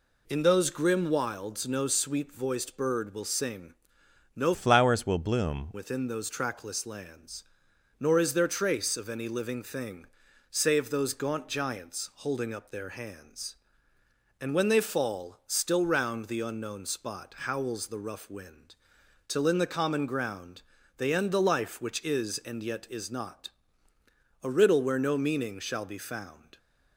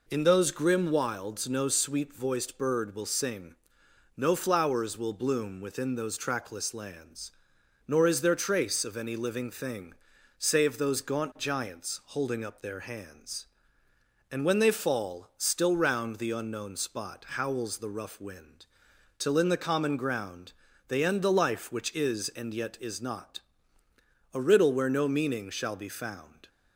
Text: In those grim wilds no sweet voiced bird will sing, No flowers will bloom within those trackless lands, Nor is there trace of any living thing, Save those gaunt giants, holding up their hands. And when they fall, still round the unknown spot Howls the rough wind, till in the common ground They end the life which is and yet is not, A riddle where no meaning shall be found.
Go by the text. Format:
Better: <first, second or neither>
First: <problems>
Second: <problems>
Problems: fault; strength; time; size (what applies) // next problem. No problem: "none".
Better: second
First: changes voice from "flowers" to "bloom"; from 4.5 to 5.7 s; 1.2 s long // pauses between "ground" and "They"; slight; at 20.6 s; 0.36 s long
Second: pauses between "ground" and "They"; slight; at 20.5 s; 0.36 s long